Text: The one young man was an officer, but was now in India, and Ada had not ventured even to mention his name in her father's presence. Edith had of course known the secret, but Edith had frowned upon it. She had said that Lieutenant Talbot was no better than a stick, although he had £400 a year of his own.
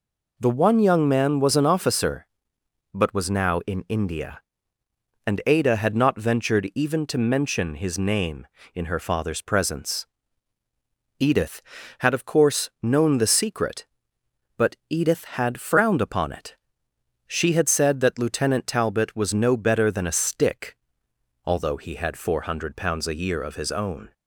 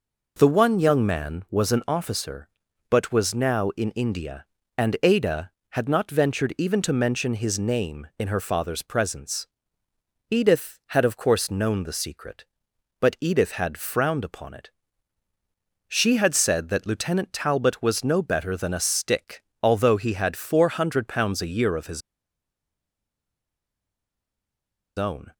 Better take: first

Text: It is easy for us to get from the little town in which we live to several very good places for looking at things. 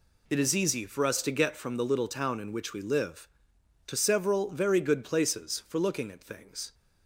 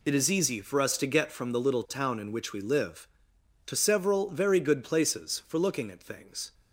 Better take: neither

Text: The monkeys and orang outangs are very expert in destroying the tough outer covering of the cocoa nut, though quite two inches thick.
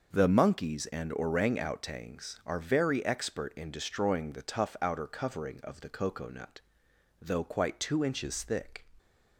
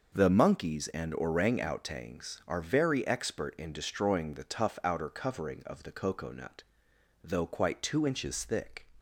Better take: neither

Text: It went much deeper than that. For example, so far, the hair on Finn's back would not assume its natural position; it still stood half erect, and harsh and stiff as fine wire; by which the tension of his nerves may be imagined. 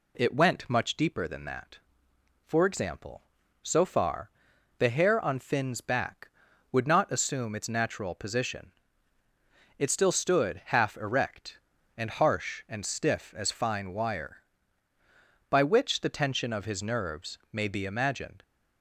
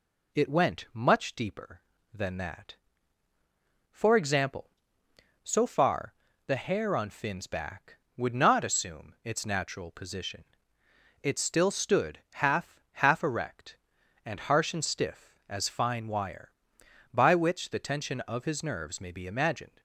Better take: first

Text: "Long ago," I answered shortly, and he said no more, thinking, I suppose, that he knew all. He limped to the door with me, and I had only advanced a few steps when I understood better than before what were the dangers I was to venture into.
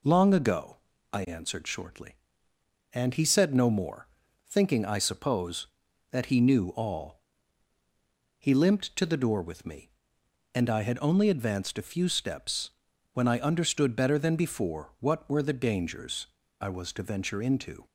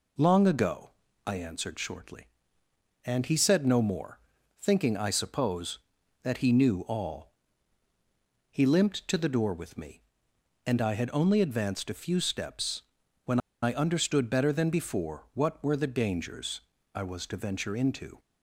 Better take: first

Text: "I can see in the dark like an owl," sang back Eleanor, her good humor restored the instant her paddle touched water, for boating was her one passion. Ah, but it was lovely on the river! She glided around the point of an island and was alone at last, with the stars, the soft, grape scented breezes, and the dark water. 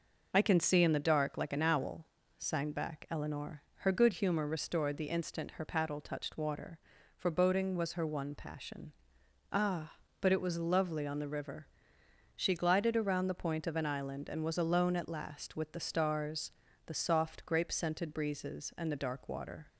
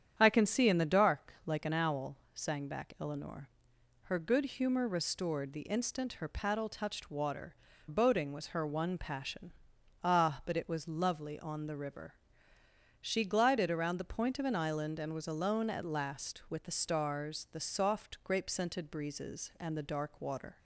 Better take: first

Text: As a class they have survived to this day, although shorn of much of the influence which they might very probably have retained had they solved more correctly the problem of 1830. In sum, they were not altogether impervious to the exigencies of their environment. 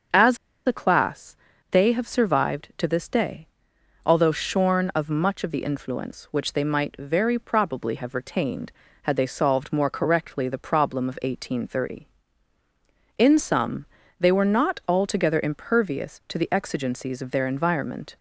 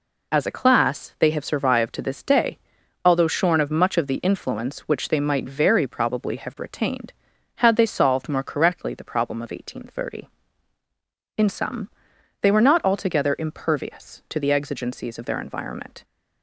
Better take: second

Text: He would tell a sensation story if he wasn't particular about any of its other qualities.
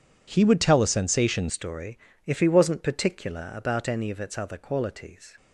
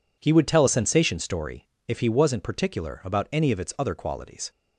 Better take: second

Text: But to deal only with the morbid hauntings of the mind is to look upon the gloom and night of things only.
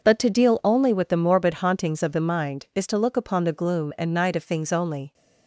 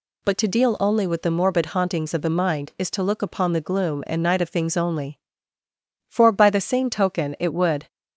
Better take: first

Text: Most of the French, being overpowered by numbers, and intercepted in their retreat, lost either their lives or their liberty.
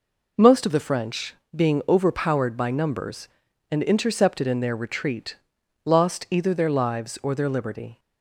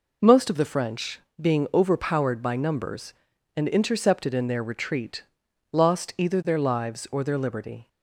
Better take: neither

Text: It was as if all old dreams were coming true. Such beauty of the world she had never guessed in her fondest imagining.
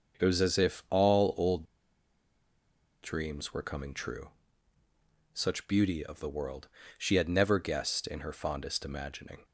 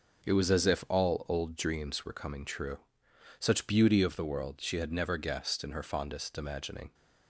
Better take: second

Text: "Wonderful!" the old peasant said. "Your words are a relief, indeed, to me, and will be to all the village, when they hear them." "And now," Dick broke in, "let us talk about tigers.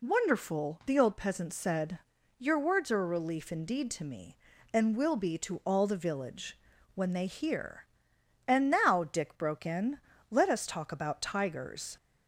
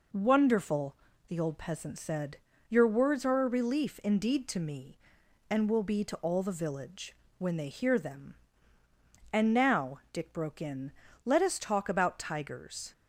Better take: second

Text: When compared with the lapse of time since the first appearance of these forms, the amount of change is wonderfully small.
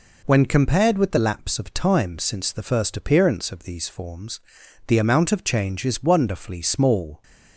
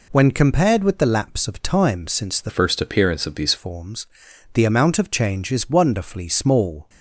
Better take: first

